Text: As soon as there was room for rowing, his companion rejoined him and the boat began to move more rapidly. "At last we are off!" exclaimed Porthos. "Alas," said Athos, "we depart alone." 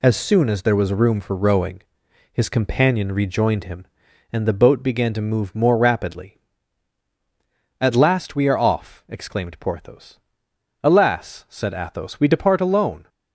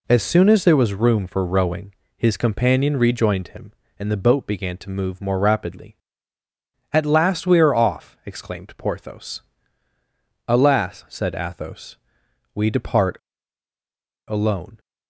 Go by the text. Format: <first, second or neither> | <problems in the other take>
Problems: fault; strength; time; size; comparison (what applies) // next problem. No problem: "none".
first | pauses between "depart" and "alone"; at 13.1 s; 1.1 s long